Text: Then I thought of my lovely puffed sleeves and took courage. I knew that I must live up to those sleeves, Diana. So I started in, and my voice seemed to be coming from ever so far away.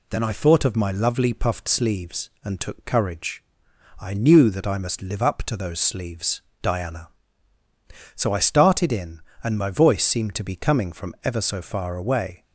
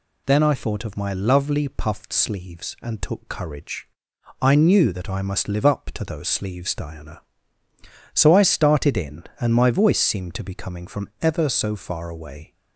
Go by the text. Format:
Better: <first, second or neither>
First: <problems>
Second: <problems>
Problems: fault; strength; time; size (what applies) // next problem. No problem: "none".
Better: neither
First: none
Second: none